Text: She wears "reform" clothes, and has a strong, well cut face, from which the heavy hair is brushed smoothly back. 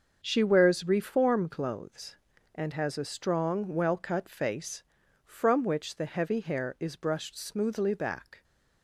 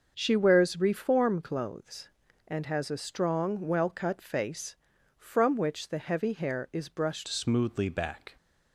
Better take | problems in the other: first | starts louder than the rest; until 1.1 s; 6.5 dB; also in the first // changes voice at "smoothly"; from 7.2 s on; 1.1 s long

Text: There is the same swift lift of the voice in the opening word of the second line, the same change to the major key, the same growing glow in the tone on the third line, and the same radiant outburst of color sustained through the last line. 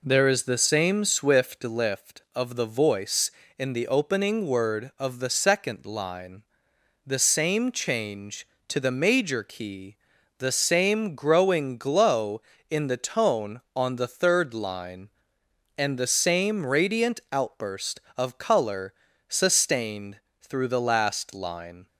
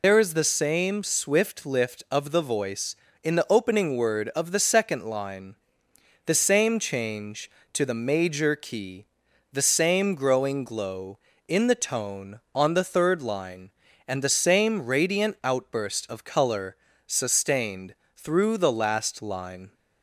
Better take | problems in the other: first | loses the start of "There"; at 0.0 s; 100 ms // pauses between "color" and "sustained"; slight; at 16.7 s; 0.32 s long; slight in the first // pauses between "sustained" and "through"; slight; at 17.9 s; 0.22 s long; slight in the first

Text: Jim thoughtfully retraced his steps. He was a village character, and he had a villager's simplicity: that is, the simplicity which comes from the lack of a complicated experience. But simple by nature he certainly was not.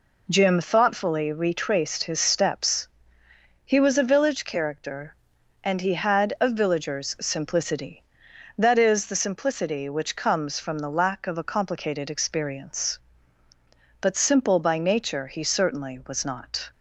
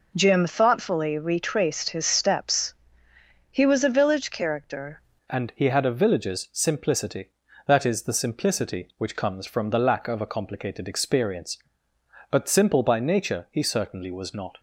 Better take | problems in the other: first | changes voice at "and"; from 5.2 s on; 9.3 s long

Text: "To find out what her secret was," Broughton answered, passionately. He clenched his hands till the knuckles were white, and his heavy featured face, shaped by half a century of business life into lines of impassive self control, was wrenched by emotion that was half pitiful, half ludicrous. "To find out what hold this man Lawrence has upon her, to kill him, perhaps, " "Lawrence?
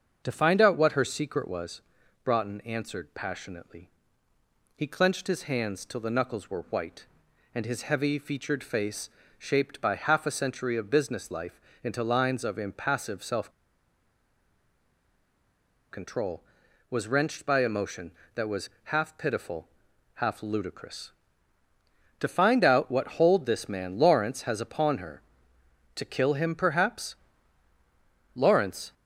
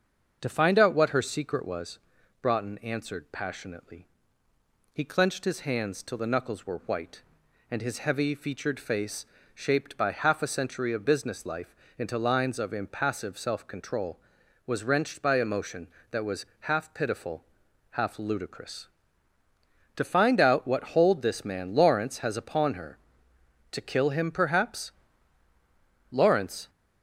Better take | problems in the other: second | starts louder than the rest; until 1.2 s; 6.5 dB; also in the second // pauses between "life" and "into"; slight; at 11.6 s; 0.22 s long; slight in the second // pauses between "self" and "control"; strong; at 13.5 s; 2.4 s long // pauses between "was" and "half"; slight; at 18.6 s; 0.16 s long; slight in the second

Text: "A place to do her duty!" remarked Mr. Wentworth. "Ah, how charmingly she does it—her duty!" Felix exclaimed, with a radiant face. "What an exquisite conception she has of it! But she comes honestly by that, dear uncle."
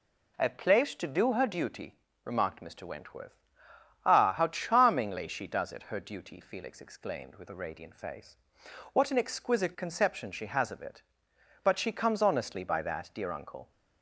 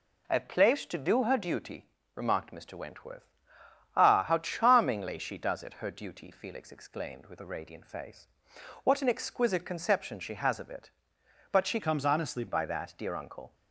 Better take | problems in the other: first | changes voice from "comes" to "honestly"; from 11.7 to 12.4 s; 0.7 s long

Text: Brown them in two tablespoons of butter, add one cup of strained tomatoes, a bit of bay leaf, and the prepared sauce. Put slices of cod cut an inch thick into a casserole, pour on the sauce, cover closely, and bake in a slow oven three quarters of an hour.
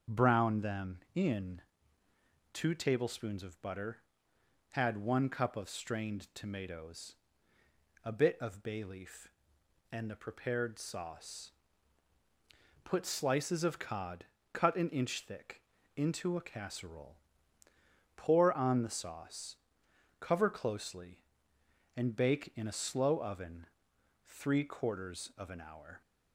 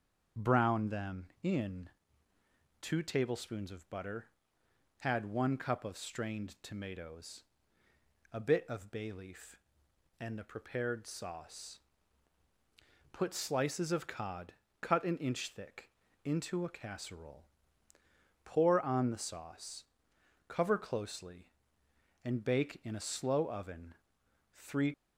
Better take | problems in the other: first | starts louder than the rest; strong; until 1.5 s; 7 dB; also in the first // pauses between "in" and "two"; noticeable; at 1.8 s; 0.90 s long; noticeable in the first // pauses between "cod" and "cut"; slight; at 14.5 s; 0.26 s long; slight in the first // pauses between "thick" and "into"; slight; at 15.8 s; 0.34 s long; slight in the first // pauses between "oven" and "three"; noticeable; at 23.9 s; 0.58 s long; noticeable in the first // stops before "quarters of an hour"; at 24.9 s

